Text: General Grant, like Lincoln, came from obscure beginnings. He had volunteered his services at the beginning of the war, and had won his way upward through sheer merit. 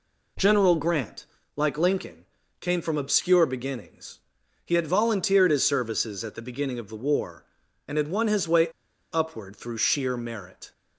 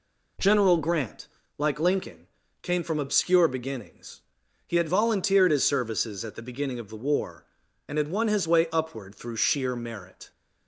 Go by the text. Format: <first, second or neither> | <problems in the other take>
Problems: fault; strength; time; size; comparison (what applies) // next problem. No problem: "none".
second | pauses between "way" and "upward"; noticeable; at 8.6 s; 0.46 s long